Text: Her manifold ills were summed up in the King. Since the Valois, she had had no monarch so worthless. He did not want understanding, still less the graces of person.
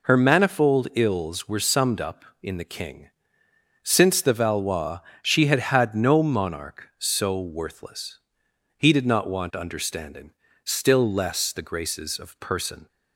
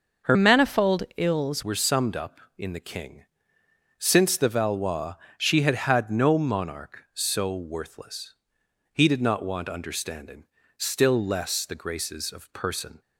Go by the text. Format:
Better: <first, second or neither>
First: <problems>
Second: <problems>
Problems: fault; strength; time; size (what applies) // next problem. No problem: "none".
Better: first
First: none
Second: starts louder than the rest; noticeable; until 1.4 s; 6 dB // changes voice from "manifold" to "ills"; from 0.3 to 1.6 s; 1.3 s long